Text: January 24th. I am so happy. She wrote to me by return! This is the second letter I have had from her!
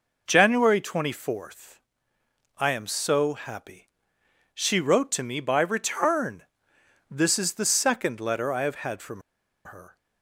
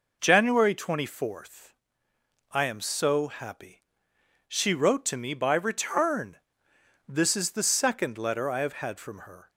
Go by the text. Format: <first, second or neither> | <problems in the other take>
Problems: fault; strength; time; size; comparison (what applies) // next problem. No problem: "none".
second | pauses between "from" and "her"; at 9.1 s; 0.45 s long